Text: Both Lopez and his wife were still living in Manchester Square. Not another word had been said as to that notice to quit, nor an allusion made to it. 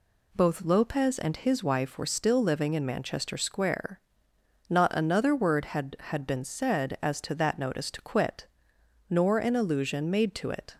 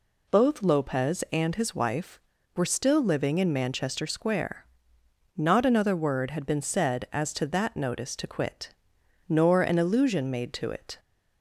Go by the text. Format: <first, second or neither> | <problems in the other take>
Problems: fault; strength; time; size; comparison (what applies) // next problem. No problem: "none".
second | says "had" twice; at 5.9 s